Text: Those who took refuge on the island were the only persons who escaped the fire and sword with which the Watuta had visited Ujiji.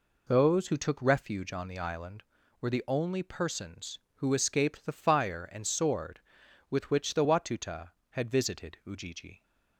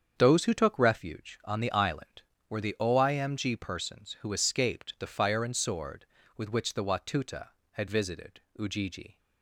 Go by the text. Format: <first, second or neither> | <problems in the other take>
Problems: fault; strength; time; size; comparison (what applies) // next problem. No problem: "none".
first | starts louder than the rest; strong; until 1.1 s; 7.5 dB // says "oimg" for "only"; at 2.8 s // pauses between "visited" and "Ujiji"; slight; at 8.3 s; 0.18 s long